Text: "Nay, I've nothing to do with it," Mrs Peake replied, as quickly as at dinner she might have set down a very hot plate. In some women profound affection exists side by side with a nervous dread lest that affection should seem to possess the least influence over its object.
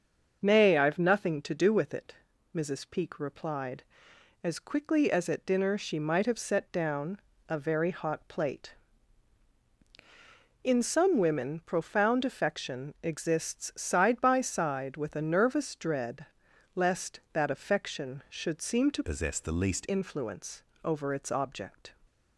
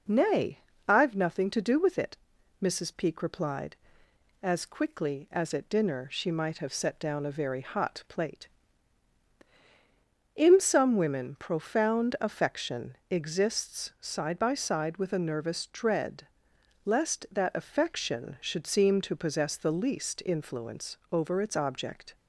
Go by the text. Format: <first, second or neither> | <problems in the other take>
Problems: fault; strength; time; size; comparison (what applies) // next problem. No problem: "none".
second | starts louder than the rest; until 1.4 s; 6.5 dB // pauses between "down" and "a"; slight; at 7.1 s; 0.30 s long // pauses between "dread" and "lest"; noticeable; at 16.2 s; 0.50 s long; noticeable in the second // changes voice from "possess" to "least"; from 19.0 to 19.8 s; 0.8 s long // pauses between "influence" and "over"; slight; at 20.6 s; 0.22 s long; slight in the second